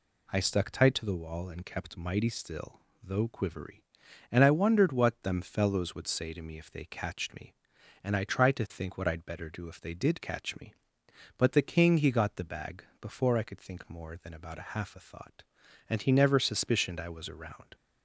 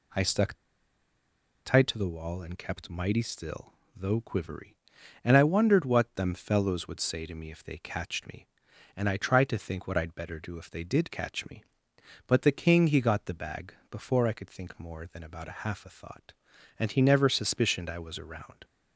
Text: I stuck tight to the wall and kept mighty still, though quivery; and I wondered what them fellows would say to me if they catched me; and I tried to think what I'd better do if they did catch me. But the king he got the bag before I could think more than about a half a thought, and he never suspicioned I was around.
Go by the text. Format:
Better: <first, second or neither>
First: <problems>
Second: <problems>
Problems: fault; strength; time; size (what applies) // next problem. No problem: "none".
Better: first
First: pauses between "bag" and "before"; slight; at 12.8 s; 0.16 s long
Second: pauses between "stuck" and "tight"; at 0.5 s; 1.1 s long // pauses between "bag" and "before"; slight; at 13.7 s; 0.16 s long